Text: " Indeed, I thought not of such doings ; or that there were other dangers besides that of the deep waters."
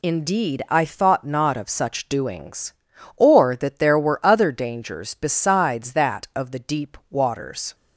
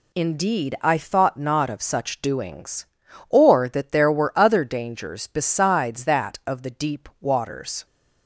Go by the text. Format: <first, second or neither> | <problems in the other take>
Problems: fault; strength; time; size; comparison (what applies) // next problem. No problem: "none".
neither | none